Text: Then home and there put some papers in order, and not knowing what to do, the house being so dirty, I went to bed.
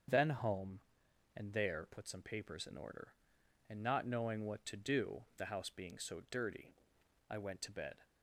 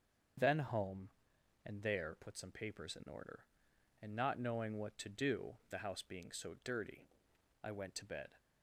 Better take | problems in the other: neither | starts louder than the rest; strong; the same in both

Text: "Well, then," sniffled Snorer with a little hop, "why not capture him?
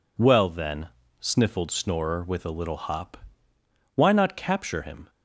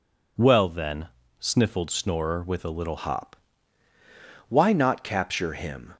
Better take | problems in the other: first | changes voice at "hop"; from 2.9 s on; 3.0 s long

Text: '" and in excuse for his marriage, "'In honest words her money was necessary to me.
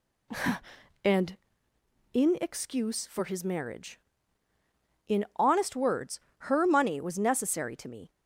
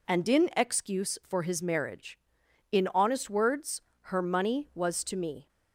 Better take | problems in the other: first | pauses between "words" and "her"; slight; at 3.8 s; 0.20 s long; slight in the first // skips "necessary"; at 5.0 s

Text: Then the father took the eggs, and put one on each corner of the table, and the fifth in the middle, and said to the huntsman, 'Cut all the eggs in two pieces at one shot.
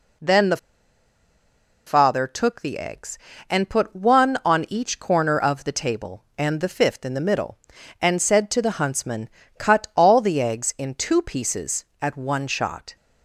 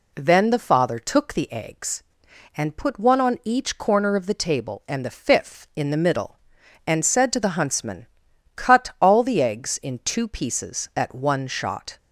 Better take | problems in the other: second | pauses between "the" and "father"; strong; at 0.5 s; 1.2 s long

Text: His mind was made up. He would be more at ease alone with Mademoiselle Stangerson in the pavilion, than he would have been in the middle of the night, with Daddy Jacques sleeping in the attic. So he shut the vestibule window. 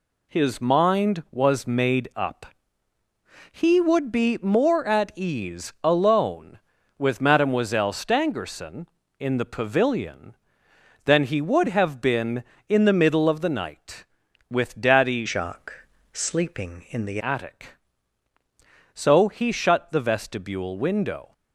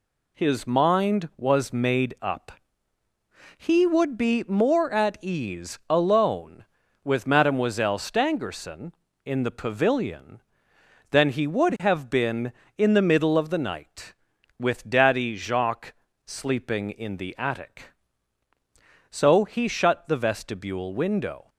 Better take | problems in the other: second | changes voice from "Jacques" to "the"; from 15.2 to 17.1 s; 1.9 s long // pauses between "Jacques" and "sleeping"; slight; at 15.8 s; 0.30 s long; slight in the second

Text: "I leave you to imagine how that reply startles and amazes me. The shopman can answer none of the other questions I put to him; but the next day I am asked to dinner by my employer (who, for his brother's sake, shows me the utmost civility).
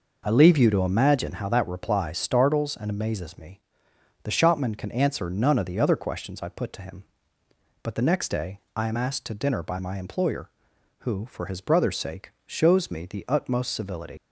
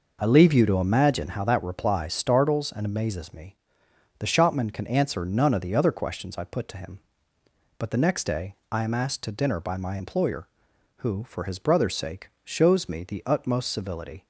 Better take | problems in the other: second | leaves "civility" unfinished; at 14.1 s; 90 ms

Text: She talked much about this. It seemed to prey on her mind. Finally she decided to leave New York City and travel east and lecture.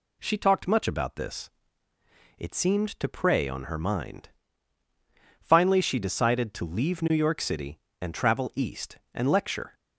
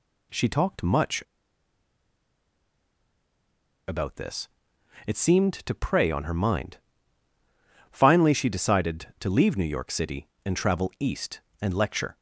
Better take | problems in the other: first | pauses between "much" and "about"; strong; at 1.2 s; 2.6 s long

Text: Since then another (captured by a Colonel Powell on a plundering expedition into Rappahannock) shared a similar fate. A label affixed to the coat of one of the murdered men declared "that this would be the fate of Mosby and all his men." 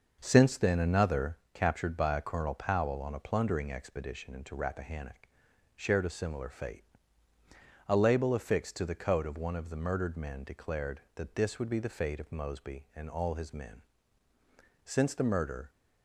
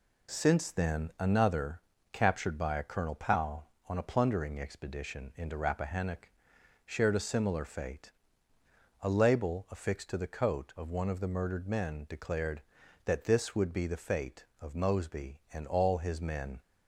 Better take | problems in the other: second | starts louder than the rest; until 1.2 s; 6.5 dB // goes on to say "Since the murder"; noticeable; from 14.8 s on; 0.86 s long

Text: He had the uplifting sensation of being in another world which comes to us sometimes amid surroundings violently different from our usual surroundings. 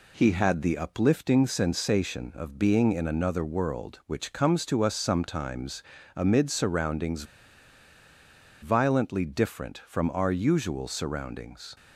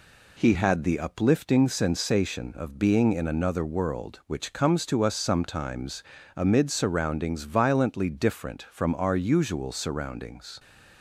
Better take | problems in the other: second | pauses between "sometimes" and "amid"; slight; at 5.8 s; 0.32 s long; slight in the second // pauses between "surroundings" and "violently"; strong; at 7.2 s; 1.3 s long

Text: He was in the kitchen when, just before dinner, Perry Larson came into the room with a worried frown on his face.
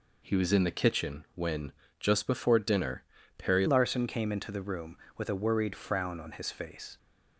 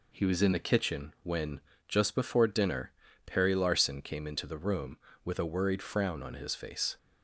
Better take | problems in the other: second | changes voice at "Larson"; from 3.6 s on; 3.3 s long

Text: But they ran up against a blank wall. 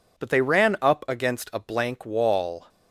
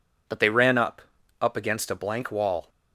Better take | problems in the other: first | says "up" twice; at 1.4 s

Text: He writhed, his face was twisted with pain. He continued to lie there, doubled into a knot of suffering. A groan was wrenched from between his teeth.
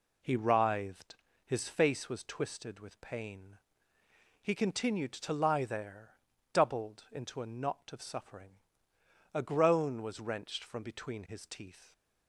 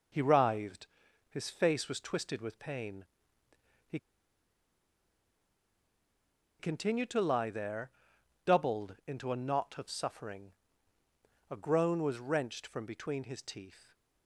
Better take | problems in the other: first | pauses between "He" and "continued"; strong; at 3.9 s; 2.6 s long

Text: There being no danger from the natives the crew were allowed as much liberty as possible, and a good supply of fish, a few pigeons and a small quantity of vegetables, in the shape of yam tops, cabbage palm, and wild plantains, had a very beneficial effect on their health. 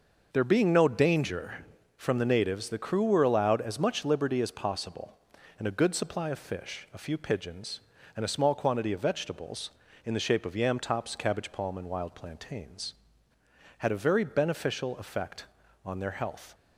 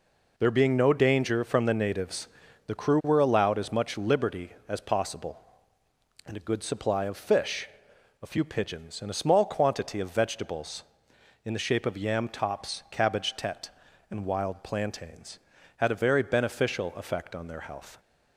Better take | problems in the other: first | pauses between "natives" and "the"; at 2.2 s; 0.38 s long // says "tete" for "palm"; at 13.3 s

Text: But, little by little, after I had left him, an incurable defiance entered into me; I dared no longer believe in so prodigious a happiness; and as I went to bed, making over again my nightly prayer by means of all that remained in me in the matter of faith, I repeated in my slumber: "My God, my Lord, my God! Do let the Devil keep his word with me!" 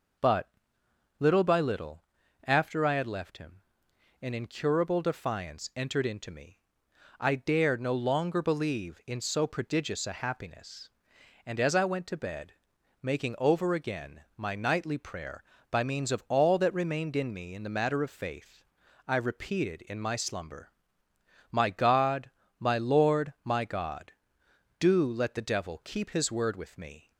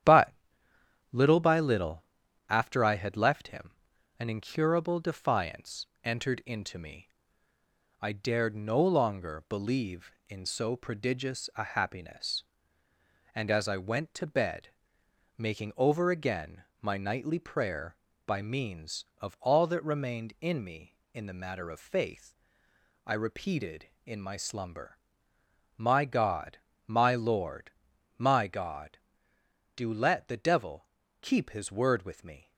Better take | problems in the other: first | gets quieter; noticeable; throughout; 5.5 dB // pauses between "defiance" and "entered"; slight; at 5.8 s; 0.18 s long // pauses between "again" and "my"; slight; at 16.6 s; 0.18 s long // pauses between "Devil" and "keep"; slight; at 30.8 s; 0.36 s long

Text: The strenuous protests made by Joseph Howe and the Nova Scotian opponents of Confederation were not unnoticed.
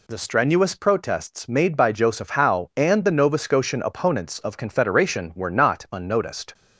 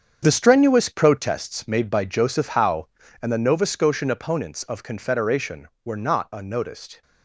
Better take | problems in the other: first | gets quieter; strong; throughout; 11 dB

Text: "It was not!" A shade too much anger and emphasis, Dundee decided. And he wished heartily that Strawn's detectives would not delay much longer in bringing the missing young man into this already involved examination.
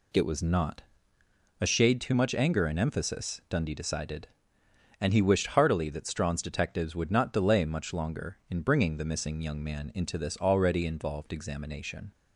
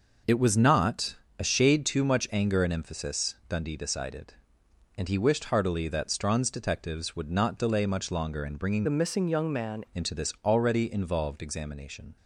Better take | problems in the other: first | changes voice from "the" to "man"; from 8.8 to 9.8 s; 1.0 s long

